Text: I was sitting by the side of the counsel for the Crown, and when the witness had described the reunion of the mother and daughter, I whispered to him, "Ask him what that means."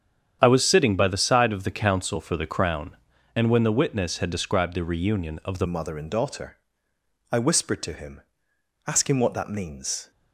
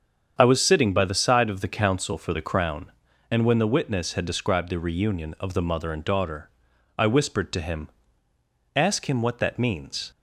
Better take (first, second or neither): second